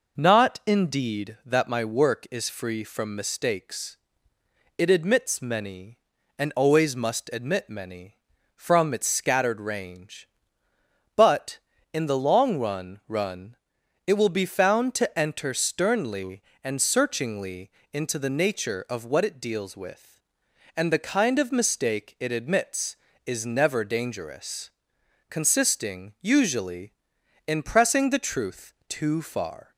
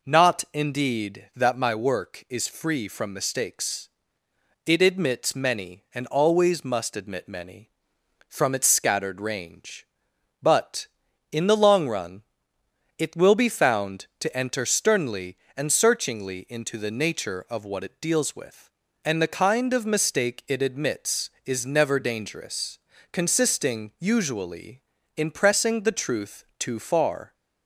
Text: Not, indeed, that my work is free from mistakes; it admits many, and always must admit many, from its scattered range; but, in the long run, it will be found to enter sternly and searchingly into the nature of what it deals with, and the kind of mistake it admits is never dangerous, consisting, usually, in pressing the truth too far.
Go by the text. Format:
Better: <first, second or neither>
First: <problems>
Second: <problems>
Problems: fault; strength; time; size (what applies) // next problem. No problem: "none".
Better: second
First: says "run" twice; at 13.0 s // pauses between "searchingly" and "into"; slight; at 17.6 s; 0.22 s long // pauses between "truth" and "too"; slight; at 28.7 s; 0.16 s long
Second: none